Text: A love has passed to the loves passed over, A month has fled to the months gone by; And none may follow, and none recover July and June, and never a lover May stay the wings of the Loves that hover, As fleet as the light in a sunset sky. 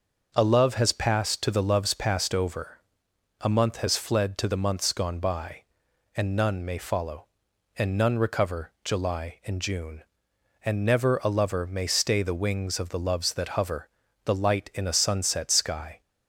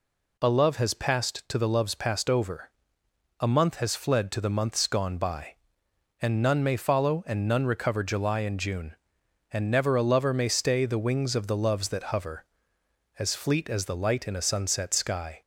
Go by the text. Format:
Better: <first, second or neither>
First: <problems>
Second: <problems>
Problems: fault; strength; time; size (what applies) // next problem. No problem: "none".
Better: second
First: starts louder than the rest; until 1.3 s; 6.5 dB // skips "As fleet as"; at 14.0 s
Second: none